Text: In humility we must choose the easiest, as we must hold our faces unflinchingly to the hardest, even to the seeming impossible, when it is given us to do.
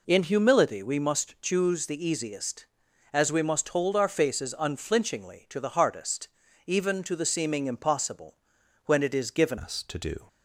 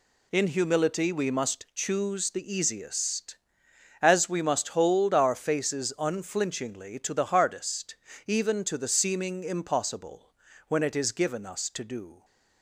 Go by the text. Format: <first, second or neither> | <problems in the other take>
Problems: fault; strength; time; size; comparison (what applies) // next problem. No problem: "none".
second | changes voice at "us"; from 9.5 s on; 0.7 s long